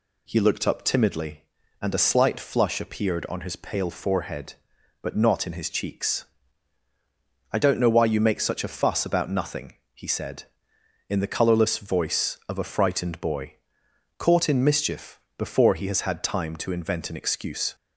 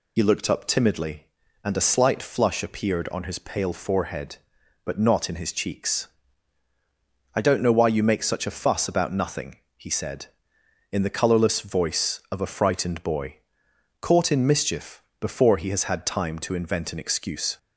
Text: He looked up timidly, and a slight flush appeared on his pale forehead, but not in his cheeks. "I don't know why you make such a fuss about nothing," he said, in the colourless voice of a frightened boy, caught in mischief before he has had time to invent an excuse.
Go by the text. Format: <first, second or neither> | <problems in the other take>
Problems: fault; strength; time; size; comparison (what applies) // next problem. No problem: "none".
first | loses the start of "He"; at 0.1 s; 65 ms // pauses between "mischief" and "before"; slight; at 15.0 s; 0.16 s long; slight in the first